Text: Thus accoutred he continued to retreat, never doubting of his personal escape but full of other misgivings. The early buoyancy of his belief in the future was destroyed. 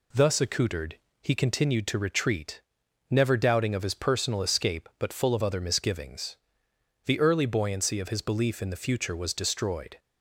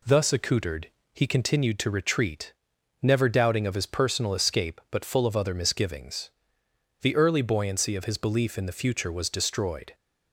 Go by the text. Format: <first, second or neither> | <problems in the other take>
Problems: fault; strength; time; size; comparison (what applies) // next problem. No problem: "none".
neither | pauses between "accoutred" and "he"; slight; the same in both